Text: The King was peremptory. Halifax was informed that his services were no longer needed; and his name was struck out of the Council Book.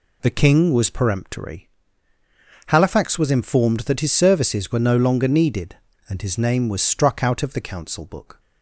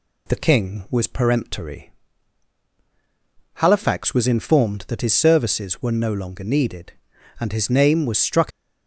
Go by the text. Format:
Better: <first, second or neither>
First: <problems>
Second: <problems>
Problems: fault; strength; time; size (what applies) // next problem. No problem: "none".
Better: first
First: none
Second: stops before "out of the Council Book"; at 8.5 s